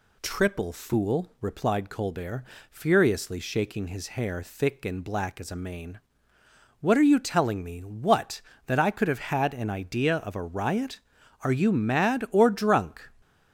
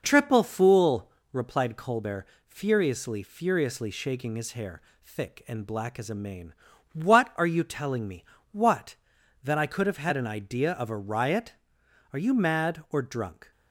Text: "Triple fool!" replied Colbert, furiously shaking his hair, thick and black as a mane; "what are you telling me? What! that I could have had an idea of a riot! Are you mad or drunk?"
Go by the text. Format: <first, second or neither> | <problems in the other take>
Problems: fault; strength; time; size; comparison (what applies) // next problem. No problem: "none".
first | says "furiously" twice; at 3.2 s